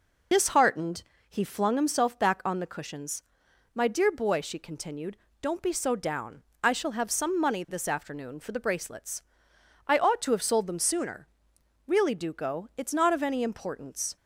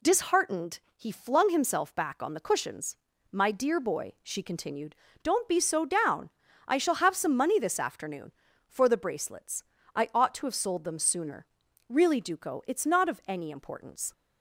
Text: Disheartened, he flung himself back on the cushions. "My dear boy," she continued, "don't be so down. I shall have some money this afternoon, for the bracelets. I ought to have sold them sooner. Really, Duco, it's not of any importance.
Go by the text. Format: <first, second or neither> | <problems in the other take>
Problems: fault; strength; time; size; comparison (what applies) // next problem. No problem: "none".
second | loses the start of "Disheartened"; at 0.3 s; 50 ms